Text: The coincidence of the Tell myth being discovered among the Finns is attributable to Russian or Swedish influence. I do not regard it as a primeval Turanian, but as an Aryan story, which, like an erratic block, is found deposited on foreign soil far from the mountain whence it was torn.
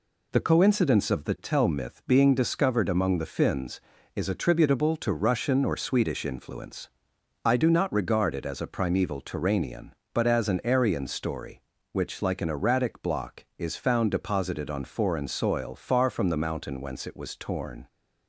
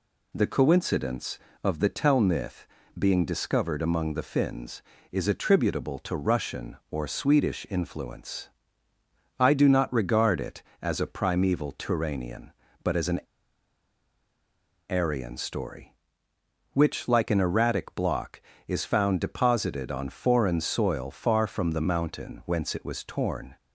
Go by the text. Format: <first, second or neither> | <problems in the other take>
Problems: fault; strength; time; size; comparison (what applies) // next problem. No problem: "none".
first | pauses between "myth" and "being"; slight; at 2.6 s; 0.30 s long // pauses between "an" and "Aryan"; strong; at 13.2 s; 1.6 s long